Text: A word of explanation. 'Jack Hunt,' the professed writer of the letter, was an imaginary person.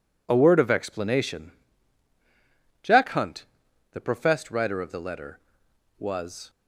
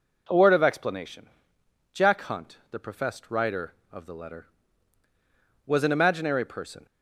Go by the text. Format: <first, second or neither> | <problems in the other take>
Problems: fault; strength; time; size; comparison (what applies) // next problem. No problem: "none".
second | stops before "an imaginary person"; at 6.4 s